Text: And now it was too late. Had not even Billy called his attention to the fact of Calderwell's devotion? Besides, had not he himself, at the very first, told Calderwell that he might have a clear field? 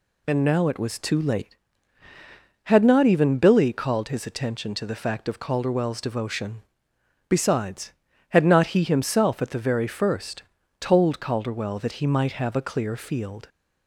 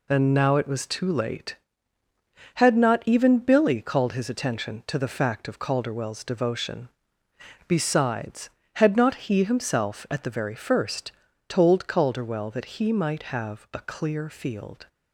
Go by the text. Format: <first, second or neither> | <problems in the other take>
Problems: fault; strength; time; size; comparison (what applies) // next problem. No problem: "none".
neither | none